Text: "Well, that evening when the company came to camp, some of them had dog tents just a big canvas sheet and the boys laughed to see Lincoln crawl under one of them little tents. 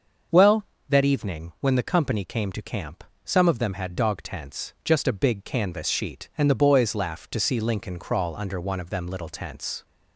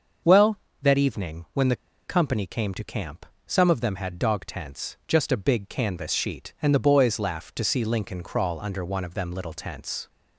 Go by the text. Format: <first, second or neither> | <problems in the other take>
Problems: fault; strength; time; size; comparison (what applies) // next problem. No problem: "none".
first | starts louder than the rest; until 1.5 s; 6.5 dB; also in the first // pauses between "the" and "company"; slight; at 1.7 s; 0.31 s long